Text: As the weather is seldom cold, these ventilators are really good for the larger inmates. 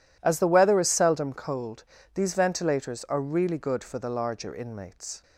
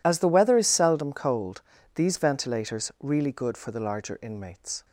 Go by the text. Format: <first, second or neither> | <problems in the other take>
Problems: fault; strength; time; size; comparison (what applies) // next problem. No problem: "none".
first | skips "are"; at 2.9 s